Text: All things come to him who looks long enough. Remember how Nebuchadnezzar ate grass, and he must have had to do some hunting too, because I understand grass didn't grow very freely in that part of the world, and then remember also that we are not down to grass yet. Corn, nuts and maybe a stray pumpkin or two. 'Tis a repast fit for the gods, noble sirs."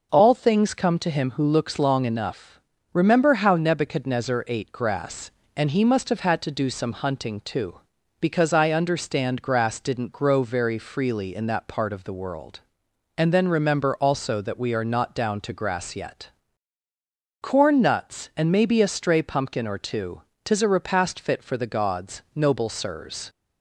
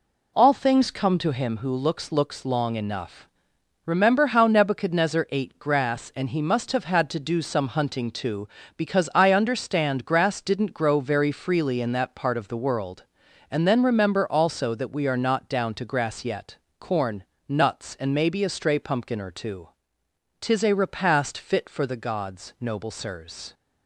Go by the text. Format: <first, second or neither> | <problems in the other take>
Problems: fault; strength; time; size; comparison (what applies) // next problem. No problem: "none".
first | says "looks" twice; at 2.1 s